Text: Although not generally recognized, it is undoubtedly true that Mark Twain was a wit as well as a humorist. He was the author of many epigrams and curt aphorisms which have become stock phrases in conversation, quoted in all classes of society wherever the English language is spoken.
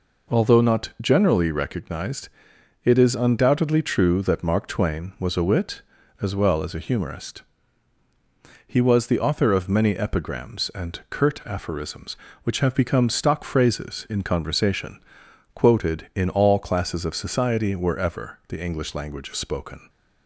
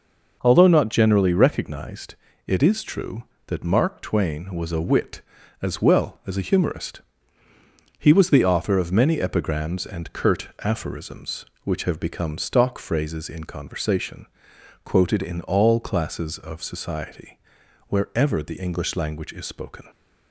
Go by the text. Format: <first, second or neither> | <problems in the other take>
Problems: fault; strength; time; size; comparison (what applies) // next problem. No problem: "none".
first | skips "undoubtedly"; at 2.8 s // pauses between "society" and "wherever"; noticeable; at 17.3 s; 0.48 s long